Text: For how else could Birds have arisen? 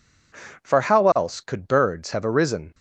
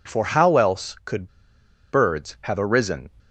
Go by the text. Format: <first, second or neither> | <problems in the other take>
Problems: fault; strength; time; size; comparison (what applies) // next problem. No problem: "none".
first | pauses between "could" and "Birds"; noticeable; at 1.2 s; 0.63 s long